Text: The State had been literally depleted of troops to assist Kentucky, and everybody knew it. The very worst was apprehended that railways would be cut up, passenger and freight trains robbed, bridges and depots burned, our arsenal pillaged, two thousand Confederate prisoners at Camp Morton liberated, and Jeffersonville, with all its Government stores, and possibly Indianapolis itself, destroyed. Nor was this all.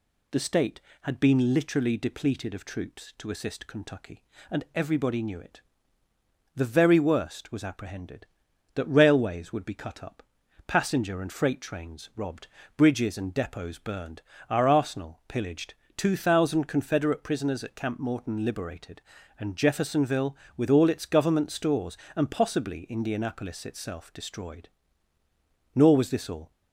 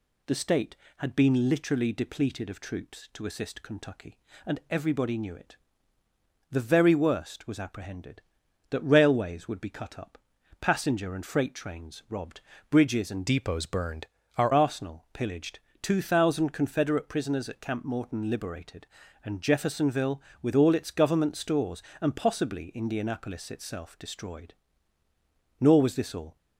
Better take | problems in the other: first | changes voice from "depots" to "our"; from 13.2 to 14.5 s; 1.3 s long

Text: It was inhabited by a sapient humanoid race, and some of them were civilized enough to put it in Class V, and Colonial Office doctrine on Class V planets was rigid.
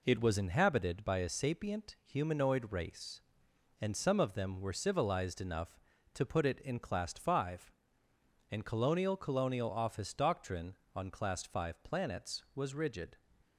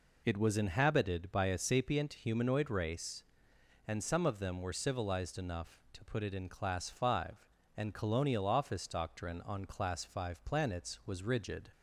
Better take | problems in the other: second | says "Colonial" twice; at 9.1 s

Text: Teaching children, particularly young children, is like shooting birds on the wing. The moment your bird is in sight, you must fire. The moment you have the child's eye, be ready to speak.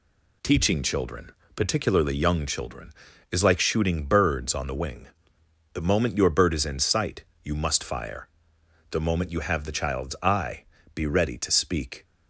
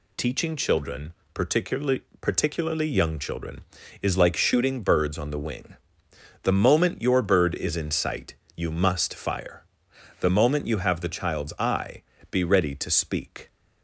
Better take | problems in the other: first | says "particularly" twice; at 2.2 s

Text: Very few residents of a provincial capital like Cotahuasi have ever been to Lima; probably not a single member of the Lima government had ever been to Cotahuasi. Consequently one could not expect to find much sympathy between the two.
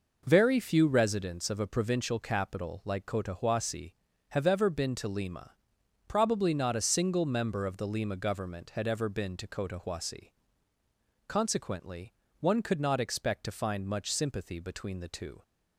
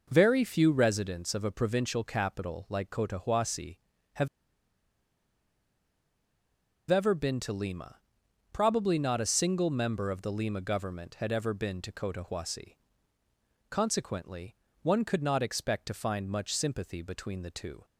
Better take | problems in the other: first | pauses between "have" and "ever"; strong; at 4.2 s; 2.6 s long // pauses between "Consequently" and "one"; slight; at 14.5 s; 0.28 s long; slight in the first

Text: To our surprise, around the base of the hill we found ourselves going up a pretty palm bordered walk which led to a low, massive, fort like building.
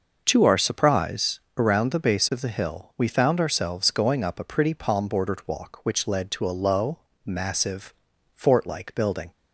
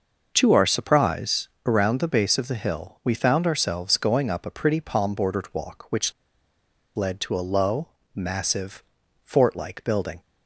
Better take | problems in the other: first | pauses between "which" and "led"; noticeable; at 6.1 s; 0.85 s long

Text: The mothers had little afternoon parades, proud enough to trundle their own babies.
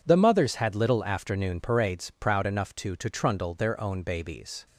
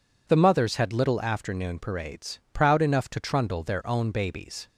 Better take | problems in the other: second | says "to" twice; at 2.9 s

